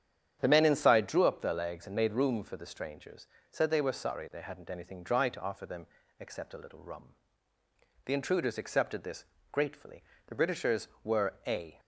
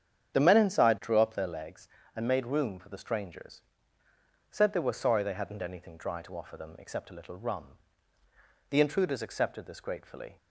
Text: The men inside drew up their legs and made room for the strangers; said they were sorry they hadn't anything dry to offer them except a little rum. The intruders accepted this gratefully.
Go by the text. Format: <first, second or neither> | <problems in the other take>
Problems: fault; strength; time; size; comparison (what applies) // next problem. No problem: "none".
second | starts louder than the rest; strong; until 1.4 s; 9 dB; strong in the second // pauses between "them" and "except"; slight; at 5.8 s; 0.32 s long // pauses between "this" and "gratefully"; slight; at 9.2 s; 0.28 s long // goes on to say "The Britishers were a"; from 10.2 s on; 1.5 s long